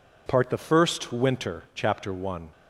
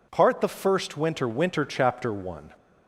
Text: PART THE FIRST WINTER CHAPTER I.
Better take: first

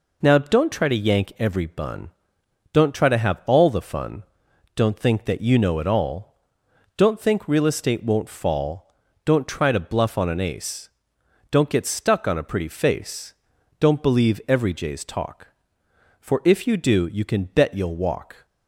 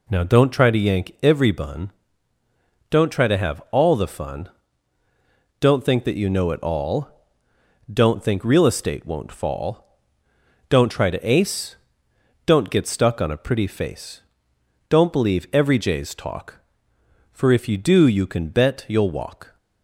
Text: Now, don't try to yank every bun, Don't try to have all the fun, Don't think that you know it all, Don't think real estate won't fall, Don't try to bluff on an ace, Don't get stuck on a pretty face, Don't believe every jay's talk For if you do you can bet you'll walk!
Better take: first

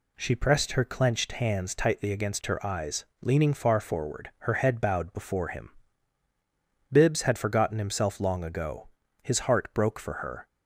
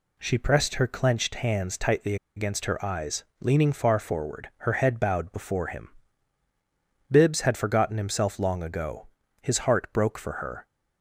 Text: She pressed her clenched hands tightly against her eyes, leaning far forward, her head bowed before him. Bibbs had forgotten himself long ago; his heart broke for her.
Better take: first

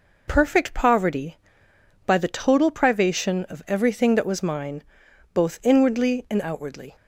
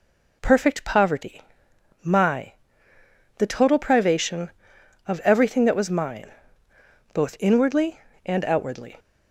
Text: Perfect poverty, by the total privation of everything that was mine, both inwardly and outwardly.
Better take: first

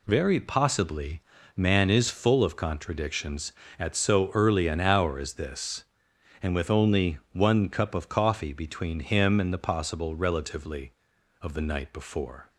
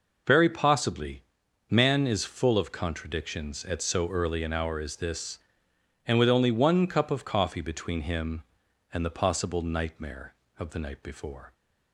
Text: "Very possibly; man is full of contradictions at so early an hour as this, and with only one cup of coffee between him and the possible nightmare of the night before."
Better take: second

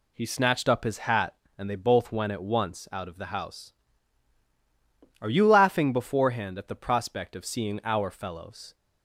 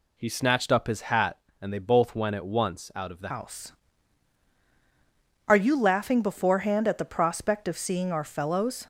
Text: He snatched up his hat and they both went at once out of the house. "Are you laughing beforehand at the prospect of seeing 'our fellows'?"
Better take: first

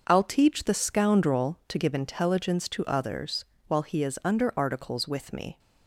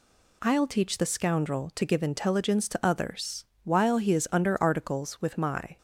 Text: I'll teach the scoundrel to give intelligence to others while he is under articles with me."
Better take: first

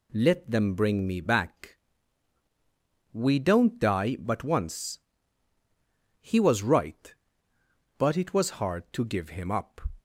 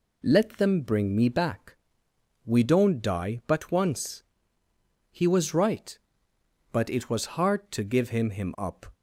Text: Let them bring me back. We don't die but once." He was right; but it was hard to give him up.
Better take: first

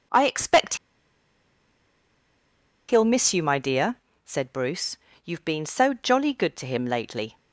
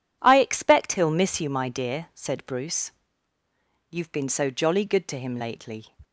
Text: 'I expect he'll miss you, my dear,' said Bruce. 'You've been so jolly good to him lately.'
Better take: second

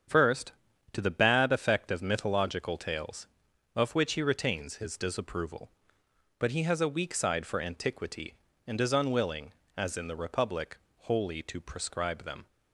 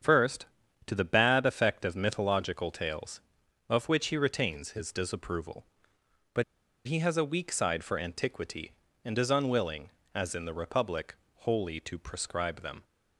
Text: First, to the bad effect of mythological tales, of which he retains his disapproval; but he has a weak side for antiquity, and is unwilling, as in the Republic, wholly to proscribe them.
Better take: first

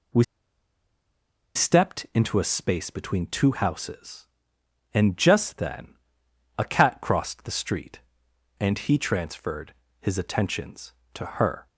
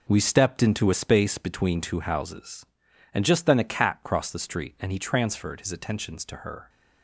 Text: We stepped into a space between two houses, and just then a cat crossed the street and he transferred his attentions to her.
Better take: second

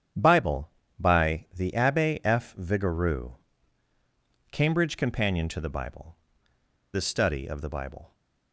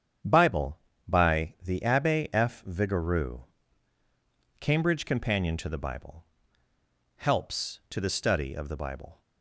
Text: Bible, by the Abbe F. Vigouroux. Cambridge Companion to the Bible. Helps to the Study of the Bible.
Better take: second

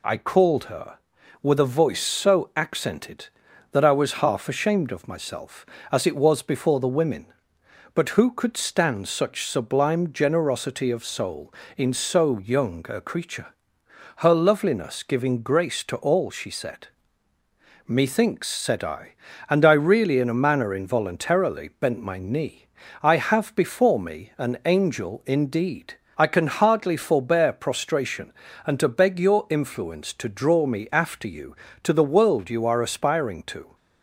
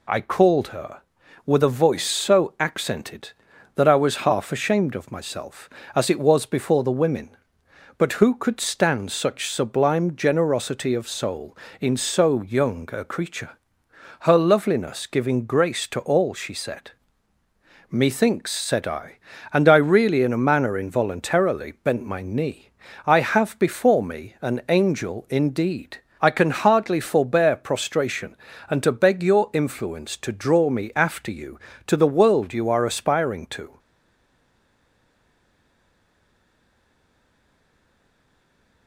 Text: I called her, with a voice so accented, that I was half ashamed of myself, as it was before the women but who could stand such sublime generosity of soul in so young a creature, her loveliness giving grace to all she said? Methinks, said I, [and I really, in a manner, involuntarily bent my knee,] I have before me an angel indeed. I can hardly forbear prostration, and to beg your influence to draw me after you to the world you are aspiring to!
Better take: first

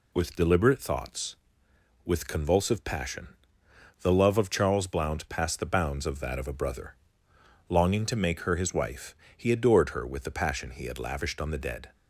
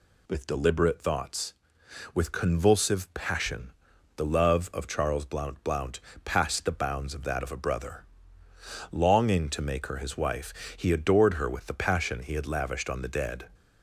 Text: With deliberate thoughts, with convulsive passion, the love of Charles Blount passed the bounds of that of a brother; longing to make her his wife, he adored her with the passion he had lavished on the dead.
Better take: first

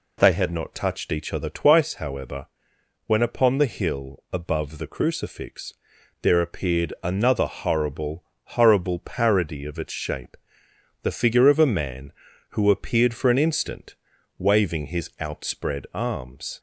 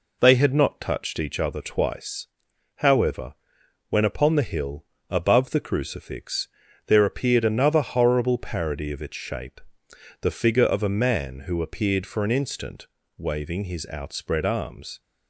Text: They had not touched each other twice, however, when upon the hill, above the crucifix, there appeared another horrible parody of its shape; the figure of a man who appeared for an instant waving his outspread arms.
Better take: second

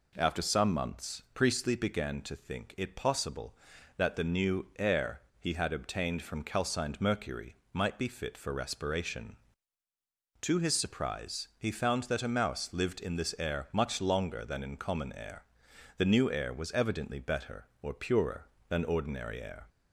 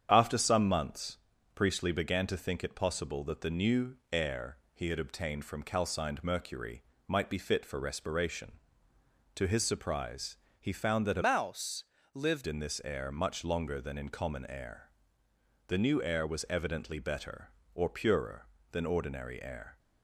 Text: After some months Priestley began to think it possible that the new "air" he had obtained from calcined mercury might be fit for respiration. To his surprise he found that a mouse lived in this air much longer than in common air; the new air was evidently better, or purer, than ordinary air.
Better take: first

